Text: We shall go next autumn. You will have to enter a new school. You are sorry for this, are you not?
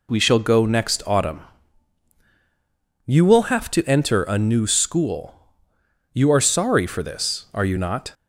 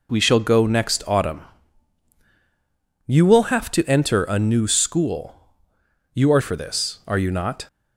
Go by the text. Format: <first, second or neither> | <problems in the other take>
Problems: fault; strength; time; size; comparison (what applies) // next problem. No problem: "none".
first | skips "sorry"; at 6.4 s